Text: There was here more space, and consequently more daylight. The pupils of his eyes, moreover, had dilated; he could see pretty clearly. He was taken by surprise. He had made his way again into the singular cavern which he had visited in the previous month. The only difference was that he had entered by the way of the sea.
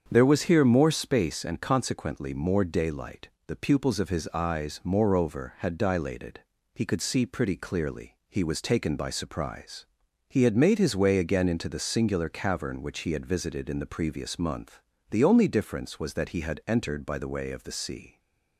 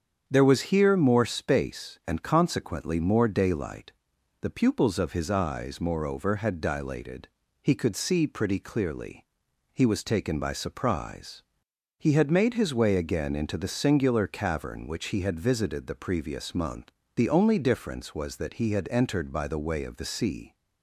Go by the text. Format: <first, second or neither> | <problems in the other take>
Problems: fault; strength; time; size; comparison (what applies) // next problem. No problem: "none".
first | starts louder than the rest; strong; until 1.2 s; 7.5 dB; strong in the first // skips "in"; at 15.8 s